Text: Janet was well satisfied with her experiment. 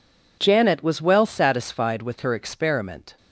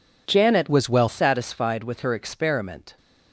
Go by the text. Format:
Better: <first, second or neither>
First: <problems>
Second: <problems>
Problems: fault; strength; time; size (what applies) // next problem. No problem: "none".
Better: first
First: none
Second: changes voice from "was" to "well"; from 0.6 to 1.0 s; 0.4 s long